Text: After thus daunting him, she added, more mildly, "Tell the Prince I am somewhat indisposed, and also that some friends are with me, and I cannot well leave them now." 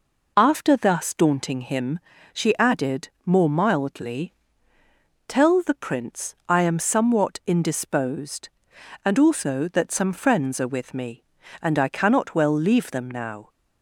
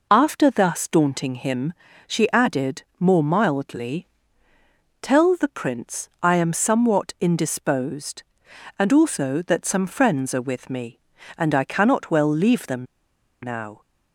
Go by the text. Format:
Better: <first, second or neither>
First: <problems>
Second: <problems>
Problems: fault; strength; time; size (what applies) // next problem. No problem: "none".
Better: first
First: none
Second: pauses between "them" and "now"; noticeable; at 12.8 s; 0.57 s long